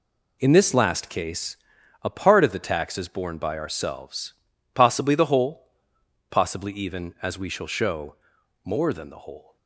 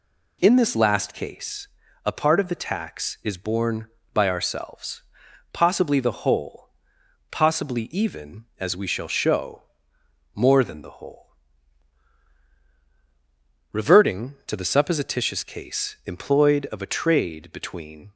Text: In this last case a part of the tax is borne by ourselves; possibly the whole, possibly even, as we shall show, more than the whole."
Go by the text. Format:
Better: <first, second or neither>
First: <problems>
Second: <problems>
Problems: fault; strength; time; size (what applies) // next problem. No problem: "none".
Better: first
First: pauses between "case" and "a"; noticeable; at 1.5 s; 0.46 s long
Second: pauses between "case" and "a"; at 1.6 s; 0.38 s long // goes on to say "Reverting to the supposititious case employed of a trade between"; strong; from 13.7 s on; 4.4 s long